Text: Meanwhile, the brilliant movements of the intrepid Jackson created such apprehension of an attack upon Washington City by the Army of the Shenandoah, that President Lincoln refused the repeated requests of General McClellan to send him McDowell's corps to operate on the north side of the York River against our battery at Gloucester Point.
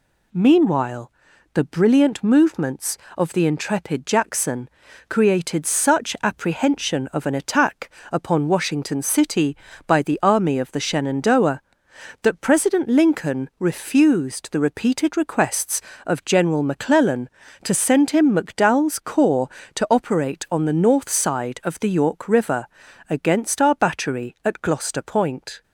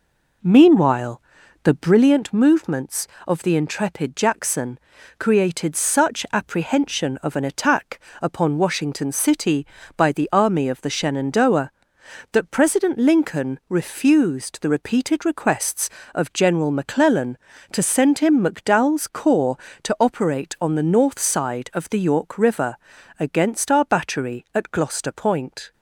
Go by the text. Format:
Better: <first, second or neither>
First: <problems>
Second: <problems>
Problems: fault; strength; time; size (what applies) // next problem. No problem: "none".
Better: first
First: pauses between "Jackson" and "created"; at 4.6 s; 0.40 s long // pauses between "attack" and "upon"; slight; at 7.9 s; 0.22 s long // pauses between "River" and "against"; at 22.6 s; 0.42 s long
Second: starts louder than the rest; until 2.1 s; 4 dB // pauses between "Jackson" and "created"; at 4.7 s; 0.40 s long // pauses between "attack" and "upon"; slight; at 7.9 s; 0.22 s long // pauses between "River" and "against"; at 22.7 s; 0.42 s long